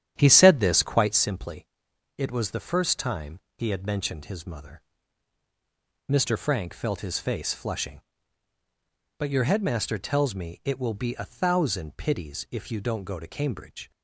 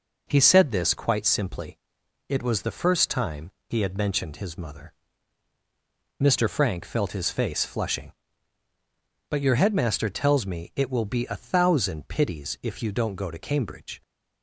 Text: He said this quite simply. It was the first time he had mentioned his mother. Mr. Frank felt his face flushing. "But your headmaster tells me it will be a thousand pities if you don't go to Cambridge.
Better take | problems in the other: second | starts louder than the rest; strong; until 1.4 s; 10.5 dB // pauses between "time" and "he"; slight; at 3.3 s; 0.20 s long; slight in the second

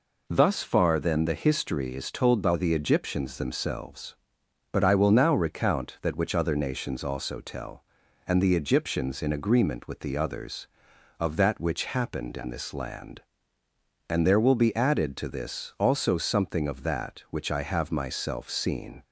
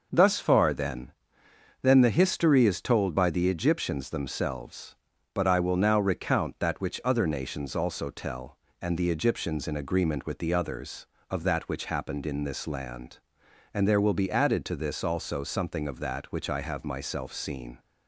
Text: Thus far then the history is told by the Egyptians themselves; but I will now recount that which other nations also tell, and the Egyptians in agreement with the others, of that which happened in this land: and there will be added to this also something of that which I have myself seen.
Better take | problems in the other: first | says "then" twice; at 1.8 s

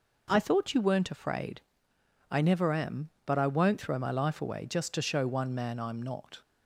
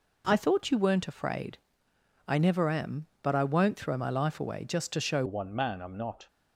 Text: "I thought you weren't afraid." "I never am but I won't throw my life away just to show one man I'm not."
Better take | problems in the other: first | changes voice at "one"; from 5.2 s on; 1.0 s long

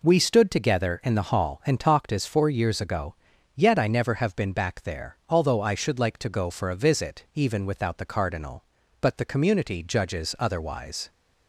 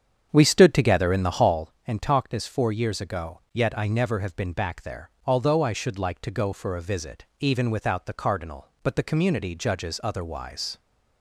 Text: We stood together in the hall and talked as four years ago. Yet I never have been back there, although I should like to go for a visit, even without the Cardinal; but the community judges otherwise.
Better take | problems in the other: first | starts louder than the rest; strong; until 1.7 s; 8 dB

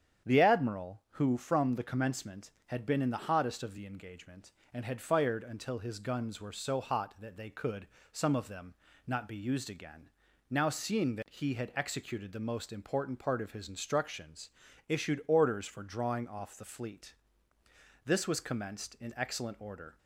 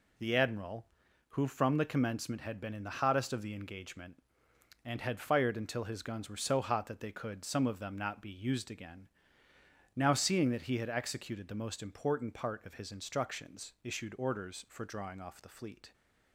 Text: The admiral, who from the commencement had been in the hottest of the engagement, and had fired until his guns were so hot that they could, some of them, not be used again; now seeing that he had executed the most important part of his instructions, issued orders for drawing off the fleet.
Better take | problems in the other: second | starts louder than the rest; strong; until 1.3 s; 8.5 dB // goes on to say "This was commenced in excellent order"; strong; from 18.0 s on; 1.9 s long

